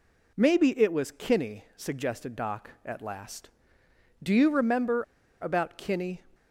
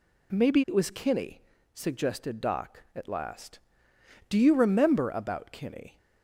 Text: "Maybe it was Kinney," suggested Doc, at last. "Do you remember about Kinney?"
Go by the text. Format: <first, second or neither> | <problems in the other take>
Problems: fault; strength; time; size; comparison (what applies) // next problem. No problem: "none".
second | pauses between "remember" and "about"; at 5.0 s; 0.37 s long